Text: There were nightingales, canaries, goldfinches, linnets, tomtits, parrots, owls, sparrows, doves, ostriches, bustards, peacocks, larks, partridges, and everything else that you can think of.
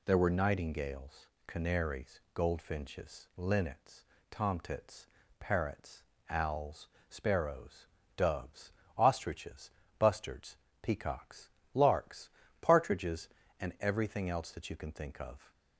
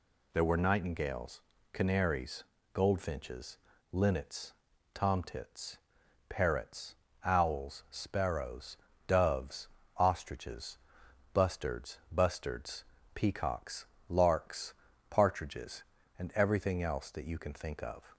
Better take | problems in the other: first | says "bustards" twice; at 12.1 s

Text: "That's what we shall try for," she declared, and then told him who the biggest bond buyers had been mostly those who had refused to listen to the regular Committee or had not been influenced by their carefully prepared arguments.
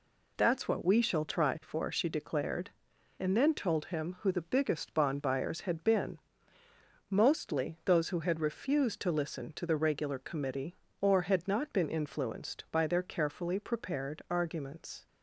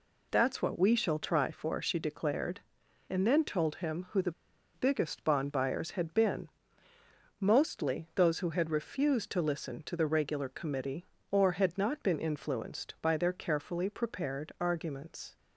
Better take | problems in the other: first | pauses between "the" and "biggest"; at 4.3 s; 0.42 s long // pauses between "been" and "mostly"; noticeable; at 6.4 s; 0.92 s long; noticeable in the first

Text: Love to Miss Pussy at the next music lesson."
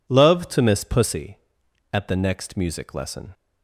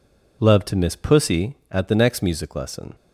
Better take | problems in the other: neither | none

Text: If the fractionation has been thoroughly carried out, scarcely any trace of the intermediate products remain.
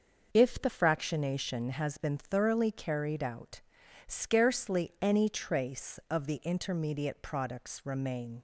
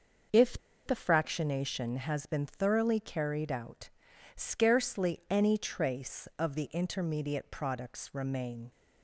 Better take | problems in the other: first | starts louder than the rest; noticeable; until 1.6 s; 6 dB; noticeable in the first // pauses between "If" and "the"; slight; at 0.5 s; 0.27 s long

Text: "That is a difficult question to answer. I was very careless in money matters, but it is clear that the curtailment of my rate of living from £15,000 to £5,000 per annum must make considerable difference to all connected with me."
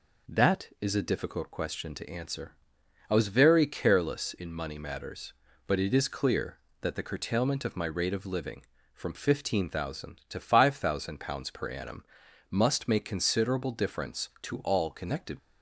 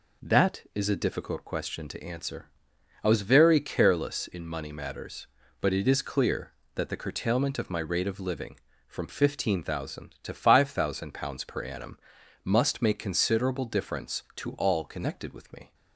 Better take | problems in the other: second | pauses between "annum" and "must"; noticeable; at 12.0 s; 0.48 s long; noticeable in the second // stops before "with me"; at 15.3 s

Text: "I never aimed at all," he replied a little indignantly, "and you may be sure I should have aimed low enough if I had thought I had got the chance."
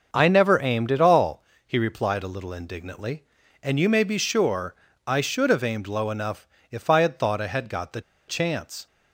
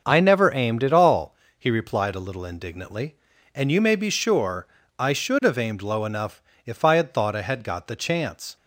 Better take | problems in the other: second | starts louder than the rest; noticeable; until 1.1 s; 6 dB; noticeable in the second // pauses between "sure" and "I"; slight; at 4.7 s; 0.32 s long; slight in the second // pauses between "enough" and "if"; slight; at 6.4 s; 0.20 s long; slight in the second // pauses between "the" and "chance"; slight; at 8.0 s; 0.26 s long

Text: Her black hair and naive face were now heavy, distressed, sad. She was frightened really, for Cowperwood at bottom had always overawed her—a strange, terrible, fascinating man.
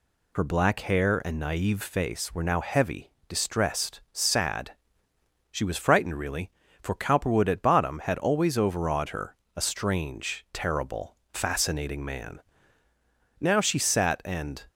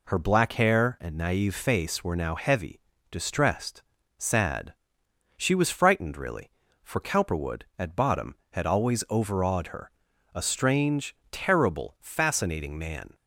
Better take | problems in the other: second | goes on to say "Now she sat and"; noticeable; from 13.4 s on; 1.2 s long

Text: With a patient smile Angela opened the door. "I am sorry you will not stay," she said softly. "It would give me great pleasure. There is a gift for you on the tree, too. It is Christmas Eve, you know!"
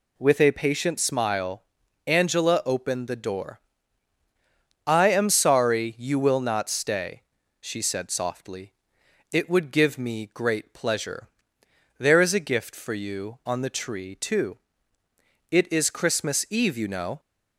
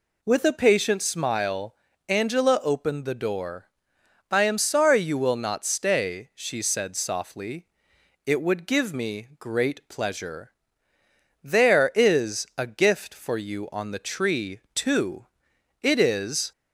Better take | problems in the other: first | pauses between "smile" and "Angela"; slight; at 1.7 s; 0.34 s long; also in the first // stops before "Christmas Eve you know"; at 16.5 s

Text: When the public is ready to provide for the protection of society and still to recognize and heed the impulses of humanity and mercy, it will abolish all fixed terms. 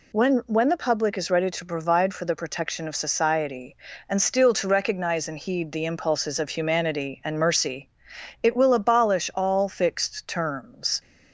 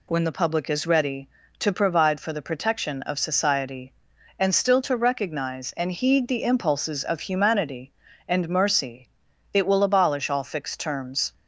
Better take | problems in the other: second | says "When" twice; at 0.4 s

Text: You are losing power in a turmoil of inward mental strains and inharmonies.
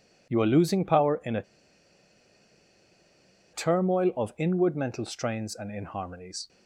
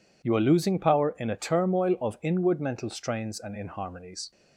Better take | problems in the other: second | pauses between "a" and "turmoil"; strong; at 1.4 s; 2.1 s long

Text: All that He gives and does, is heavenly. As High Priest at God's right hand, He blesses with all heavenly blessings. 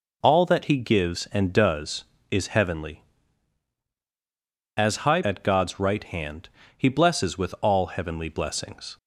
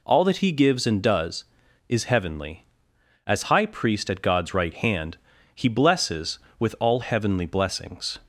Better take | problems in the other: second | skips "Priest"; at 5.2 s

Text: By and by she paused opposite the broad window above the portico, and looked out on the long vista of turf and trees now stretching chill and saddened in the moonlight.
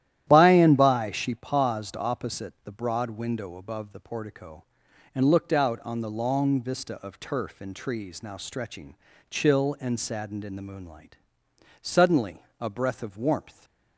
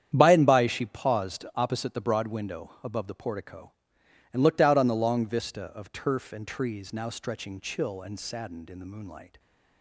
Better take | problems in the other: second | starts louder than the rest; strong; until 1.2 s; 12 dB; strong in the second // pauses between "stretching" and "chill"; slight; at 8.9 s; 0.36 s long // goes on to say "Suddenly a breath of warmth"; strong; from 11.8 s on; 1.8 s long

